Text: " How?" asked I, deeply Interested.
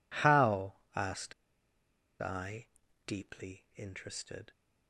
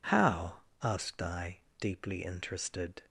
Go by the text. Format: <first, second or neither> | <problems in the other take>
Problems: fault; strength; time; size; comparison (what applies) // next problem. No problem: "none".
second | pauses between "asked" and "I"; noticeable; at 1.3 s; 0.87 s long